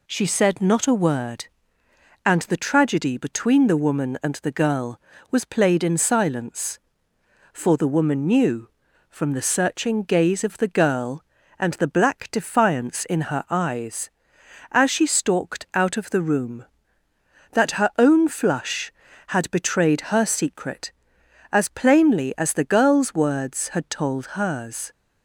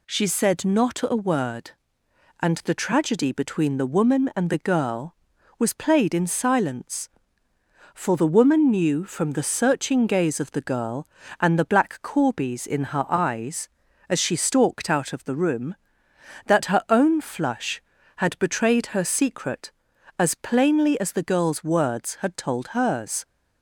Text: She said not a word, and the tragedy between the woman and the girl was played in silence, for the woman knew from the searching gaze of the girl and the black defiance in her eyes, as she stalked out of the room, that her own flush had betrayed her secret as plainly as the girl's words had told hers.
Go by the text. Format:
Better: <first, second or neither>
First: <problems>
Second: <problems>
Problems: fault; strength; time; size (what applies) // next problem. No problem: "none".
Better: first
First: none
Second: says "corbies" for "defiance"; at 12.0 s